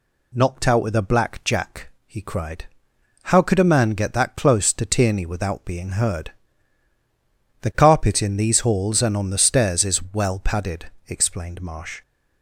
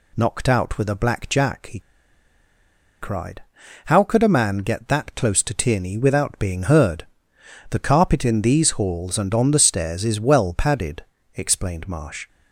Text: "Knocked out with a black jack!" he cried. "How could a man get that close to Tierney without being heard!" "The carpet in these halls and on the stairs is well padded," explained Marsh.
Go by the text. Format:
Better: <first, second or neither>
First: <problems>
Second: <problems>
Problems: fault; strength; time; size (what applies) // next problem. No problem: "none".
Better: first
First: none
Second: pauses between "he" and "cried"; at 1.8 s; 1.2 s long